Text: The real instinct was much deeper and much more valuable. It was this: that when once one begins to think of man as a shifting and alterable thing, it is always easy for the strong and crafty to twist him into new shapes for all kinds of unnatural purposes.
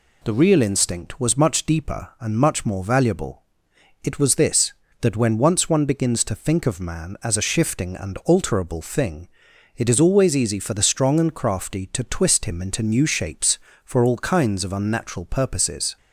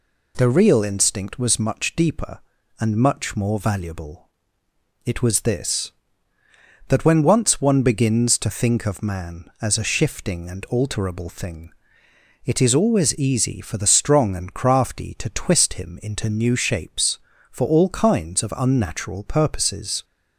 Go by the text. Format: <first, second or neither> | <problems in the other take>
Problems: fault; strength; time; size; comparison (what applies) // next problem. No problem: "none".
neither | none